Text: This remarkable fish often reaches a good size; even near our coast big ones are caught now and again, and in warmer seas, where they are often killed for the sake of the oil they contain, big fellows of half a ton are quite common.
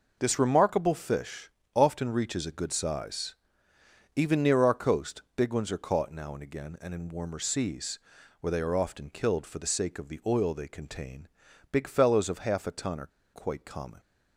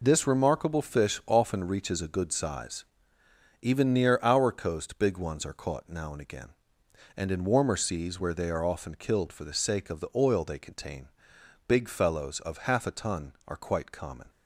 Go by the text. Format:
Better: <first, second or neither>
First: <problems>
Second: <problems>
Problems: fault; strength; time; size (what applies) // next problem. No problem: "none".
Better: second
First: pauses between "fish" and "often"; slight; at 1.4 s; 0.28 s long // pauses between "are" and "quite"; slight; at 13.1 s; 0.25 s long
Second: none